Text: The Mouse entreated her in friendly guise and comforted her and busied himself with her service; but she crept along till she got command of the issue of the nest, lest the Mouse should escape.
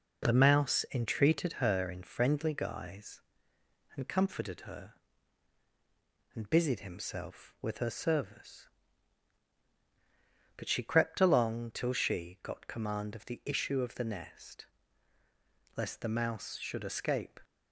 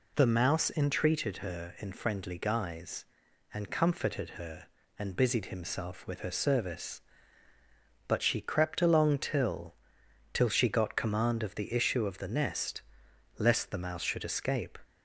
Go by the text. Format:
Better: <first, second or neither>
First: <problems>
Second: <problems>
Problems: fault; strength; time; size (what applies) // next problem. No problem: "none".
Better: first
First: none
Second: says "till" twice; at 10.3 s